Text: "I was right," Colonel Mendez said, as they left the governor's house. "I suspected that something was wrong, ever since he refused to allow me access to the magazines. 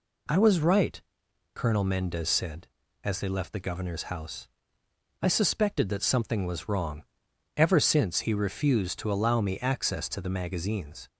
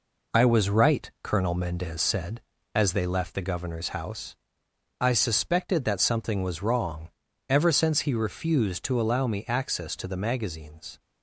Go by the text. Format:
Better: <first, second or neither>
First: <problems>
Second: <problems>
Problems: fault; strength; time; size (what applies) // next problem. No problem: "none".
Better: first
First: none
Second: gets quieter; noticeable; throughout; 4.5 dB